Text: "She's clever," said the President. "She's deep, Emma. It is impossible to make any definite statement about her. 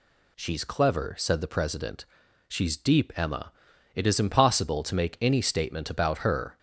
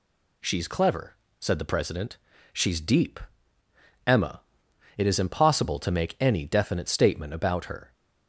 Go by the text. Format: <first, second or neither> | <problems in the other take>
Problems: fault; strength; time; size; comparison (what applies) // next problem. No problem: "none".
second | skips "definite"; at 5.4 s